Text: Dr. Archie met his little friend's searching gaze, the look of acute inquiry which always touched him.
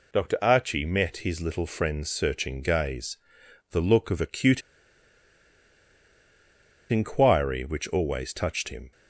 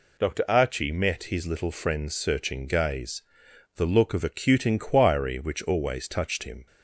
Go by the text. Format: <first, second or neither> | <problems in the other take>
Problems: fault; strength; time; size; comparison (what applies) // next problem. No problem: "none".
second | pauses between "acute" and "inquiry"; strong; at 4.6 s; 2.2 s long